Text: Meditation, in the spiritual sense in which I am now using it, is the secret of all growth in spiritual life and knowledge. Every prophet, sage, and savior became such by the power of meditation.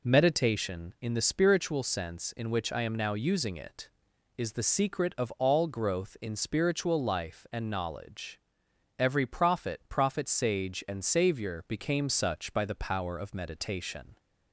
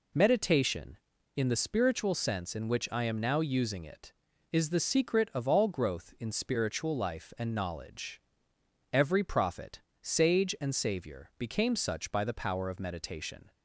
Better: second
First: says "prophet" twice; at 9.8 s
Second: none

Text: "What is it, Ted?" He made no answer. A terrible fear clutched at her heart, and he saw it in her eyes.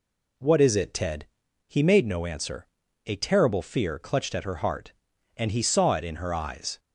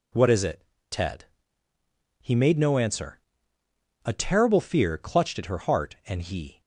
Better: first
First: none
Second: stops before "saw it in her eyes"; at 6.6 s

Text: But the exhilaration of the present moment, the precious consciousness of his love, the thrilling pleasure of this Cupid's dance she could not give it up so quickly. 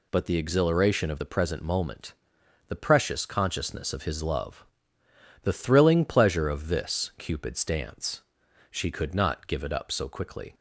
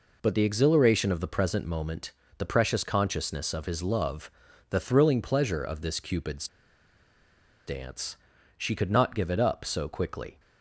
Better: first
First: pauses between "dance" and "she"; noticeable; at 8.2 s; 0.48 s long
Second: pauses between "Cupid's" and "dance"; at 6.4 s; 1.1 s long // pauses between "dance" and "she"; at 8.1 s; 0.44 s long

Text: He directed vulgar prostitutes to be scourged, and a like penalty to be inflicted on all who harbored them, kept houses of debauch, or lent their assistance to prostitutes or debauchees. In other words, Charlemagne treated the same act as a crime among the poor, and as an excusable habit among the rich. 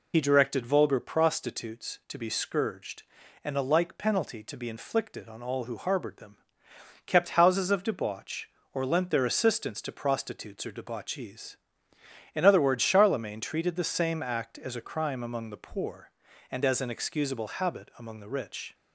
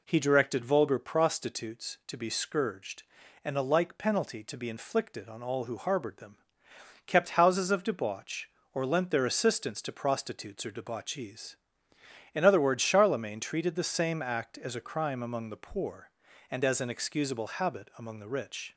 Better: second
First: loses the start of "He"; at 0.1 s; 70 ms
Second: none

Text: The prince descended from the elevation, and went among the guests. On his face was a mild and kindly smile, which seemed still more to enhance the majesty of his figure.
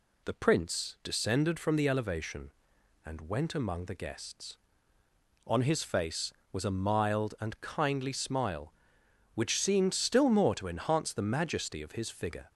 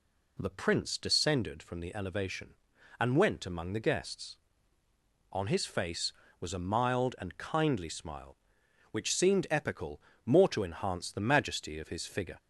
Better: first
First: none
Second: says "epical" for "still"; at 9.4 s

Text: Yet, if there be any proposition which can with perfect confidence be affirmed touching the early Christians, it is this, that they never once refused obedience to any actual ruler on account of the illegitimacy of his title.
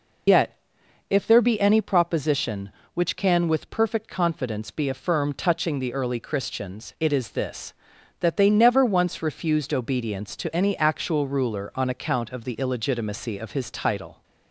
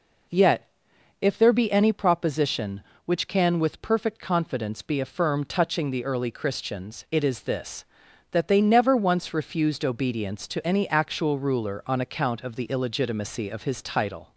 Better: second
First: loses the start of "Yet"; at 0.2 s; 85 ms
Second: none

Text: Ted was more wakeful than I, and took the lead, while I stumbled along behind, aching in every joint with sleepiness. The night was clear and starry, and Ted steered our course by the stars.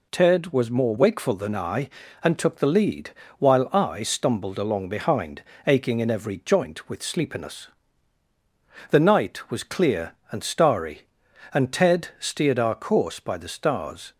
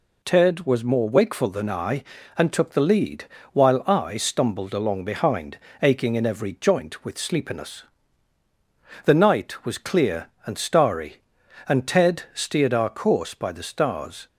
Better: neither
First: none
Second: none

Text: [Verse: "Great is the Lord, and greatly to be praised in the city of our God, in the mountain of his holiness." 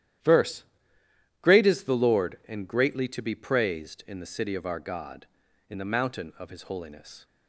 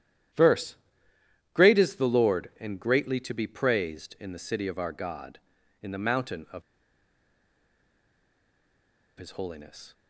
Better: first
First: starts louder than the rest; strong; until 1.9 s; 11.5 dB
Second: starts louder than the rest; strong; until 2.0 s; 11.5 dB // pauses between "of" and "his"; strong; at 6.6 s; 2.5 s long

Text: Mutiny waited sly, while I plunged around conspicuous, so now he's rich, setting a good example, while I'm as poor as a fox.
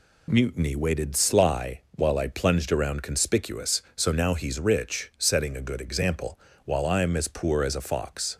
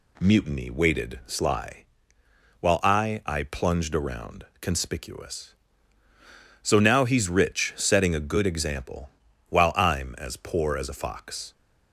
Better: first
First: none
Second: says "I" twice; at 3.2 s // pauses between "around" and "conspicuous"; slight; at 4.4 s; 0.18 s long

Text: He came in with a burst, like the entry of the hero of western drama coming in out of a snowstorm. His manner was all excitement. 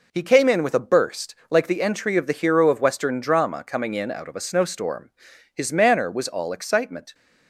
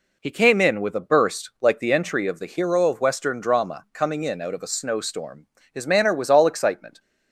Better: neither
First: none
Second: none

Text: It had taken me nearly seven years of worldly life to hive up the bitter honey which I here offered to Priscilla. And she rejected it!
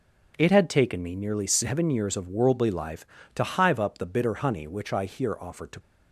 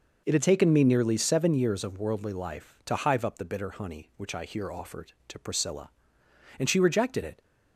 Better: second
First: stops before "Priscilla And she rejected it"; at 5.7 s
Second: none

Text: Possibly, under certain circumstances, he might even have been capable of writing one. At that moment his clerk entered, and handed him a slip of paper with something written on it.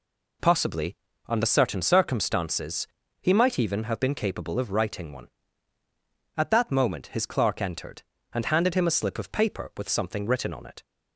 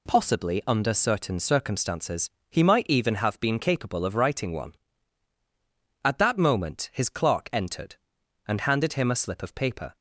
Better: first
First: none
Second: stops before "with something written on it"; at 9.9 s

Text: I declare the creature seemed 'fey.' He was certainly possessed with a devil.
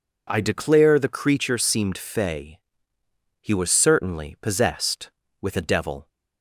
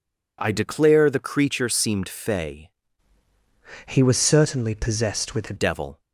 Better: first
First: none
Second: changes voice from "He" to "a"; from 3.8 to 5.5 s; 1.7 s long

